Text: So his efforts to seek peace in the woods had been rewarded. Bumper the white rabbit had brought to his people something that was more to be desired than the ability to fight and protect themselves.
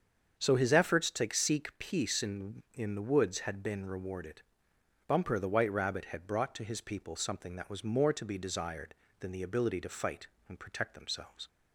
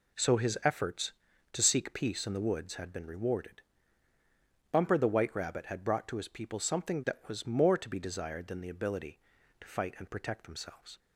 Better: second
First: starts louder than the rest; strong; until 1.4 s; 7.5 dB // says "in" twice; at 2.7 s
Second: none

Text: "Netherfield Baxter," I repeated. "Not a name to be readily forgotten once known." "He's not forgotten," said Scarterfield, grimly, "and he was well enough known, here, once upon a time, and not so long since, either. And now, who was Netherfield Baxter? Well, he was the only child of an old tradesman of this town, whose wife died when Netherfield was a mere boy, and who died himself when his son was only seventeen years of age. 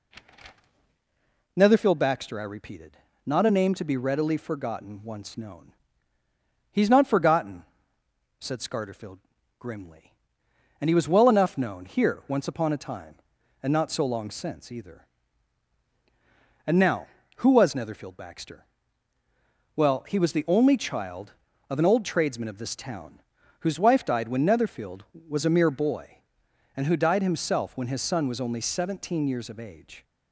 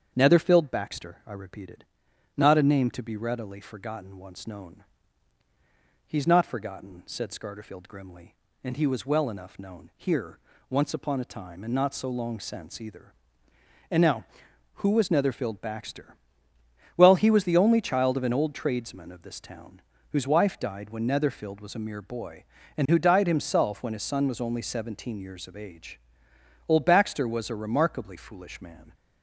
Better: first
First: none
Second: starts louder than the rest; strong; until 1.1 s; 7.5 dB // goes on to say "Old Baxter was a remarkably foolish man"; strong; from 26.6 s on; 2.2 s long

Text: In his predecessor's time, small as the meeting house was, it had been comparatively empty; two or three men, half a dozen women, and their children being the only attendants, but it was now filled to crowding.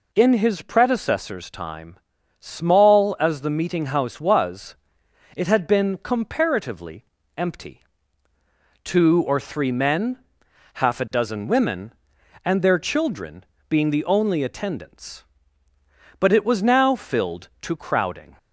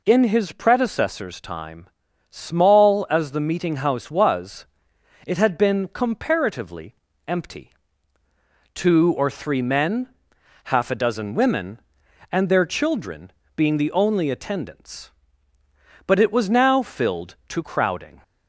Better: neither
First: pauses between "comparatively" and "empty"; slight; at 7.0 s; 0.32 s long // pauses between "children" and "being"; slight; at 13.4 s; 0.24 s long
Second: pauses between "comparatively" and "empty"; slight; at 6.9 s; 0.32 s long // pauses between "children" and "being"; slight; at 13.3 s; 0.24 s long

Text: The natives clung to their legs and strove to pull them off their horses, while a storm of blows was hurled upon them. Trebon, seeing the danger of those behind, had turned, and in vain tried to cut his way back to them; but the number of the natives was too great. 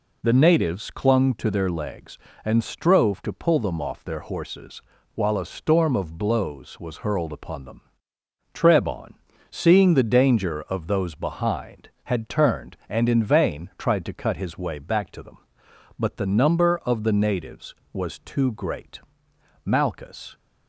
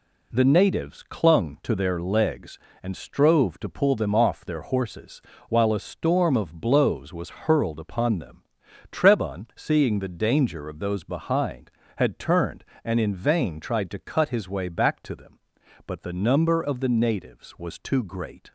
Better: second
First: goes on to say "Malchus"; noticeable; from 19.6 s on; 0.72 s long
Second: none

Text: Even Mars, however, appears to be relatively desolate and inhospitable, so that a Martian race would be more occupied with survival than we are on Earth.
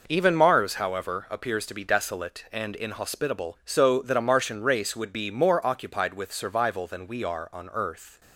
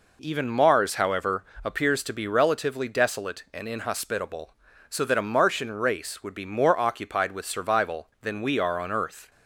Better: second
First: skips "relatively"; at 1.8 s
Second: none

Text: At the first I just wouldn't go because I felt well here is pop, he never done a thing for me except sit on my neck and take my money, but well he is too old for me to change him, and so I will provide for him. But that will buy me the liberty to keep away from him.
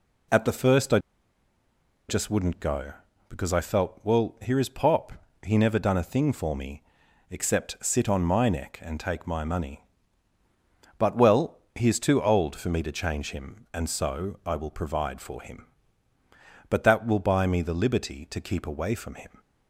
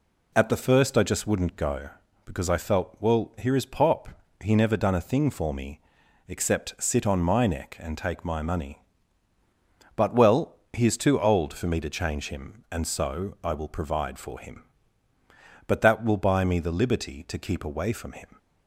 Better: second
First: pauses between "I" and "just"; at 0.9 s; 1.1 s long // pauses between "me" and "except"; noticeable; at 6.8 s; 0.48 s long // pauses between "well" and "he"; slight; at 11.5 s; 0.16 s long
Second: pauses between "me" and "except"; noticeable; at 5.7 s; 0.48 s long // pauses between "well" and "he"; slight; at 10.5 s; 0.16 s long

